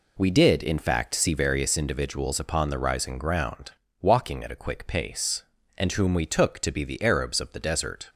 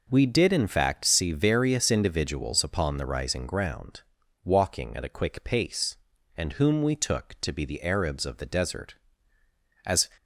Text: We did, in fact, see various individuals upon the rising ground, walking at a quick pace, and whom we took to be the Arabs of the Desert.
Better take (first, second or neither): first